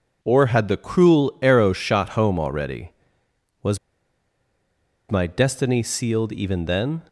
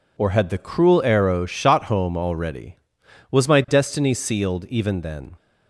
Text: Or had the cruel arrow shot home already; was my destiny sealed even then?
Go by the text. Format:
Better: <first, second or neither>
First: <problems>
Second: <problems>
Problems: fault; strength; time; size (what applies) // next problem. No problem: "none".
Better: second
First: pauses between "was" and "my"; strong; at 3.7 s; 1.3 s long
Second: none